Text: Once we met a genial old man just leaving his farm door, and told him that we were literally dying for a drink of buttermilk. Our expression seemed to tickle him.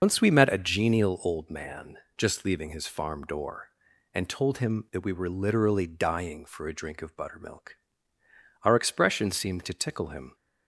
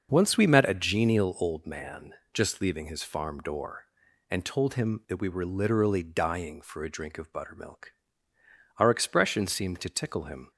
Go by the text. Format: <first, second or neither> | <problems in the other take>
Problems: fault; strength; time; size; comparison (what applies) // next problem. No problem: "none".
second | loses the start of "Once"; at 0.0 s; 95 ms // starts louder than the rest; noticeable; until 1.0 s; 6 dB; also in the second // pauses between "man" and "just"; slight; at 1.9 s; 0.22 s long; slight in the second